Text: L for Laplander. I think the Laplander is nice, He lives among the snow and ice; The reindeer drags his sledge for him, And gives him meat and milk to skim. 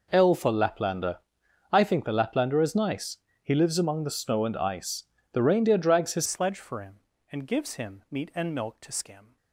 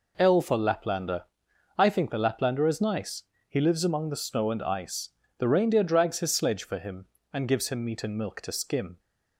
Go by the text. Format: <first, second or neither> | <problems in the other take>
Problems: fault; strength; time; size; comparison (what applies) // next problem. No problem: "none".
second | changes voice at "sledge"; from 6.2 s on; 3.1 s long